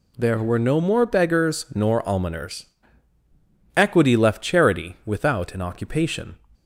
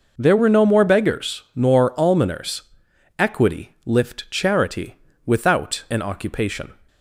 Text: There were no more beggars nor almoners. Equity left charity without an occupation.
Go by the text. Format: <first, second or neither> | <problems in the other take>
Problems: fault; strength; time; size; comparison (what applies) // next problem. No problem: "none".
first | says "lift" for "left"; at 3.8 s // pauses between "charity" and "without"; slight; at 4.9 s; 0.30 s long